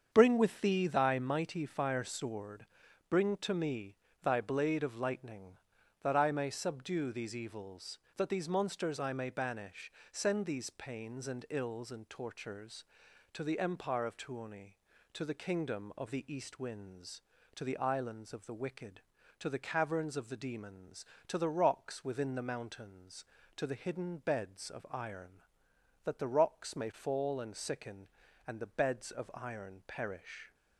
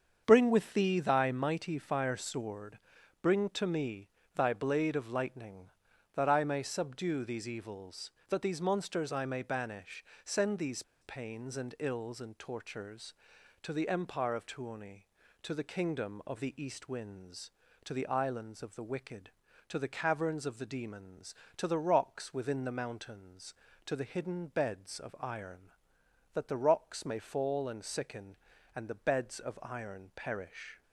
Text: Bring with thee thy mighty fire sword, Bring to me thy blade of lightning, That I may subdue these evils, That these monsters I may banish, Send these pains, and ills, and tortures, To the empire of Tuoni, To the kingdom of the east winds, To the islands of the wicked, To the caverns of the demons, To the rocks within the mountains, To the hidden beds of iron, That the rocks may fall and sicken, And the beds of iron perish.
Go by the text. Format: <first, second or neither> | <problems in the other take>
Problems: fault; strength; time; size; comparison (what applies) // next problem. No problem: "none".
first | starts louder than the rest; strong; until 1.2 s; 7 dB; strong in the first // pauses between "me" and "thy"; slight; at 4.0 s; 0.26 s long; slight in the first // pauses between "these" and "pains"; slight; at 10.8 s; 0.19 s long